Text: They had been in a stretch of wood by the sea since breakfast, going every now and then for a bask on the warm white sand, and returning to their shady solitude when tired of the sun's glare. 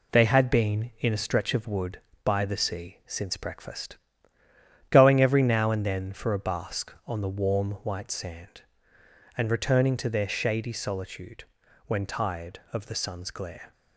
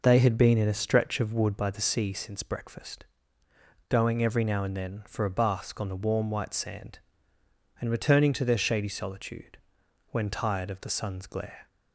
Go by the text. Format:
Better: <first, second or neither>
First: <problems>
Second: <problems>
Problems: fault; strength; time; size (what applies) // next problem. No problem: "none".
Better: neither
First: pauses between "solitude" and "when"; at 11.4 s; 0.42 s long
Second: pauses between "solitude" and "when"; noticeable; at 9.5 s; 0.48 s long